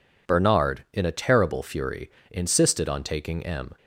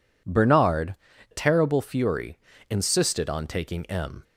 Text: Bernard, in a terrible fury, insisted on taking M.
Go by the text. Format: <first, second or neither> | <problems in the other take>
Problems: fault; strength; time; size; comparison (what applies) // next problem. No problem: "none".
first | skips "in a"; at 1.1 s